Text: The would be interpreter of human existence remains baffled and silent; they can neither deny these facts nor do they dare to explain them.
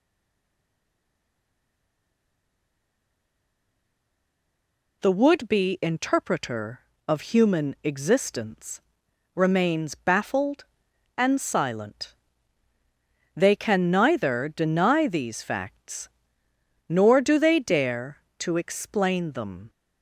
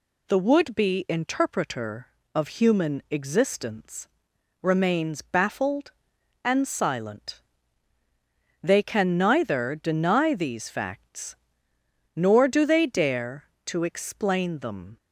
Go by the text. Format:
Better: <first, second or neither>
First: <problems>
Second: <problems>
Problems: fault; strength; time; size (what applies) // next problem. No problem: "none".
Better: second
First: stays silent before the first word; strong; until 5.0 s; 5.0 s long // pauses between "existence" and "remains"; noticeable; at 8.8 s; 0.54 s long // pauses between "facts" and "nor"; noticeable; at 16.0 s; 0.80 s long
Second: pauses between "existence" and "remains"; noticeable; at 4.0 s; 0.54 s long // pauses between "facts" and "nor"; noticeable; at 11.3 s; 0.80 s long